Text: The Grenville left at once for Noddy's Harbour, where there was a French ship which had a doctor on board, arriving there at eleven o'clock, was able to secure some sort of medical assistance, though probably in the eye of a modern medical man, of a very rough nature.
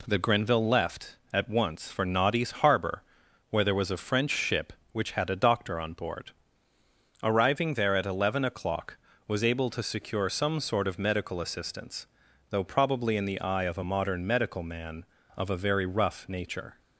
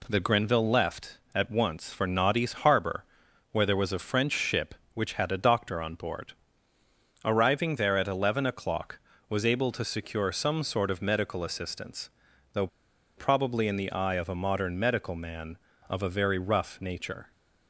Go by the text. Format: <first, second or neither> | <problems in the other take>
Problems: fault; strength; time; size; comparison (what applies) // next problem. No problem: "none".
first | pauses between "though" and "probably"; noticeable; at 12.6 s; 0.50 s long